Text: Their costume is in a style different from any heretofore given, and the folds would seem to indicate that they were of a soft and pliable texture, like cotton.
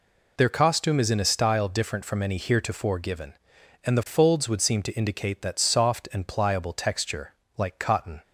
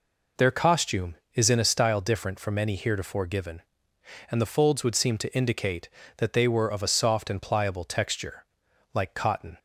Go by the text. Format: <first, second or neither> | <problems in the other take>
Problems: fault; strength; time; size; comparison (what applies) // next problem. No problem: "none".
second | skips "they were of a"; at 5.6 s